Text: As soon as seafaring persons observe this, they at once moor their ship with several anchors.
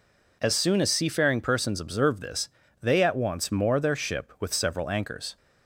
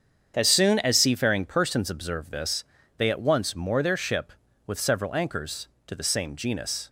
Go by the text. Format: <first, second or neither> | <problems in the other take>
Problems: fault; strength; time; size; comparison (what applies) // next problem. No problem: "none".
first | starts louder than the rest; strong; until 1.3 s; 7.5 dB // goes on to say "To the same genus"; noticeable; from 5.8 s on; 1.0 s long